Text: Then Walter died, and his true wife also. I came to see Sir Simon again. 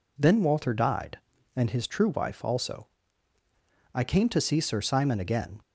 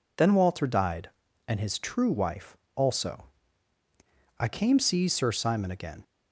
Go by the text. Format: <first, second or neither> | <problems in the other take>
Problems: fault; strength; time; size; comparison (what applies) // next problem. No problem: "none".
first | pauses between "wife" and "also"; slight; at 2.5 s; 0.20 s long // skips "to"; at 4.7 s